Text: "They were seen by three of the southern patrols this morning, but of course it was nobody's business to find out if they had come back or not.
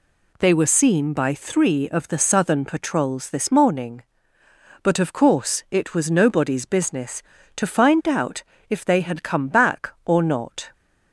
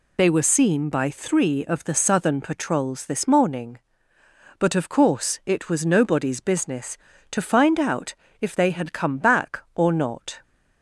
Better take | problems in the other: first | loses the start of "They"; at 0.1 s; 75 ms // pauses between "out" and "if"; slight; at 8.1 s; 0.26 s long; slight in the first

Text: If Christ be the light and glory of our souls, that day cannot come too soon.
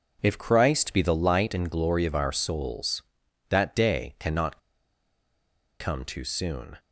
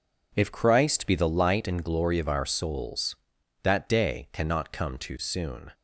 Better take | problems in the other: second | pauses between "cannot" and "come"; at 4.5 s; 1.2 s long

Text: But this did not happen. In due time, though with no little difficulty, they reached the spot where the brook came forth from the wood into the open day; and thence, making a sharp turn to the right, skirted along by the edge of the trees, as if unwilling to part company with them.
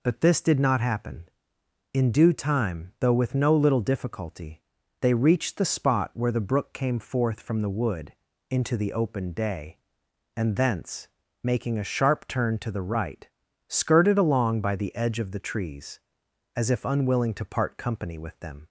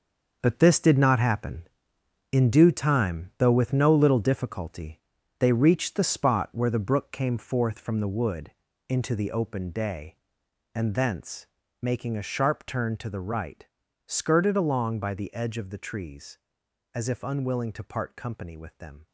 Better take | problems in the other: first | gets quieter; strong; throughout; 10 dB // pauses between "wood" and "into"; slight; at 8.5 s; 0.36 s long; slight in the first

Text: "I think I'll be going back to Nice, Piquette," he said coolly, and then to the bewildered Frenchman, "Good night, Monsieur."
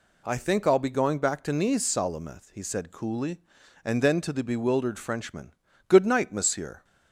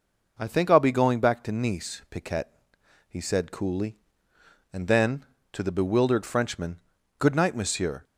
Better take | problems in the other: second | says "Salameth" for "Piquette"; at 1.8 s

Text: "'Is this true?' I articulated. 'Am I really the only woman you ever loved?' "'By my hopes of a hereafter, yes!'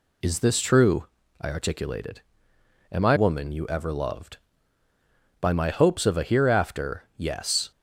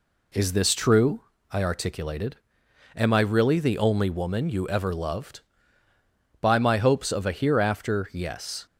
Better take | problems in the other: second | skips "really the only"; at 3.1 s

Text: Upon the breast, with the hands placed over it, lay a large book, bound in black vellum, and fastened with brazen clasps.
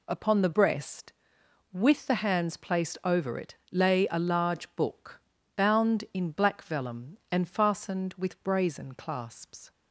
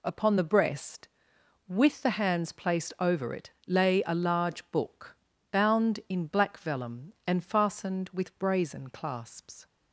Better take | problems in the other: neither | none

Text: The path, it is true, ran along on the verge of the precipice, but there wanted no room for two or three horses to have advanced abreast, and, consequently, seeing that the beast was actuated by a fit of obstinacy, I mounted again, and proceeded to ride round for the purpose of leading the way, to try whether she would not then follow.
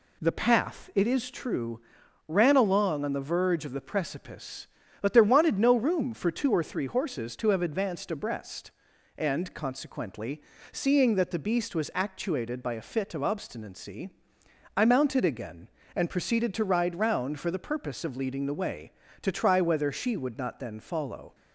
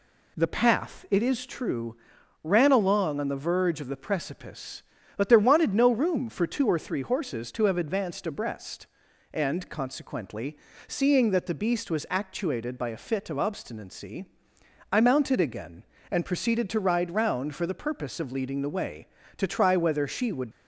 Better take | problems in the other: first | stops before "not then follow"; at 20.5 s

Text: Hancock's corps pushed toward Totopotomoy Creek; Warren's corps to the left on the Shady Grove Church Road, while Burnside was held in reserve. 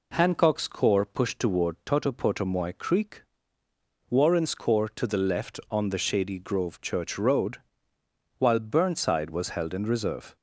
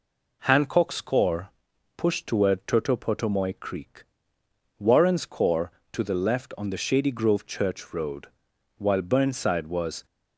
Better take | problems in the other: first | pauses between "corps" and "pushed"; noticeable; at 1.4 s; 0.48 s long // stops before "held in reserve"; at 10.0 s

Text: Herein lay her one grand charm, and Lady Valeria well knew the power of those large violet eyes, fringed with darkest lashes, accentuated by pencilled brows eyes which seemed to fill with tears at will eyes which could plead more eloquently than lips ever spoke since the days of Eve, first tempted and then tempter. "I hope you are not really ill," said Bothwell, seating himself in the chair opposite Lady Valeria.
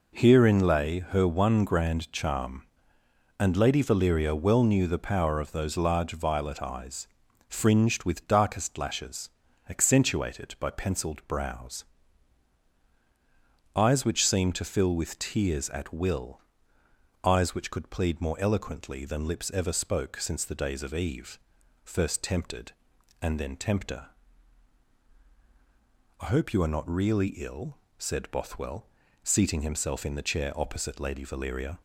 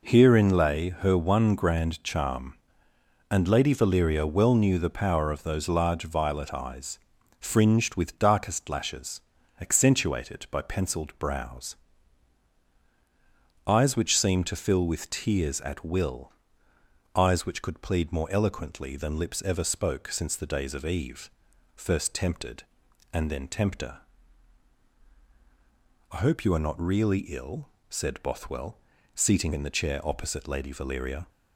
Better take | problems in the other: first | pauses between "brows" and "eyes"; strong; at 11.7 s; 1.9 s long; strong in the first // pauses between "will" and "eyes"; noticeable; at 16.3 s; 0.82 s long; noticeable in the first // skips "himself"; at 29.5 s

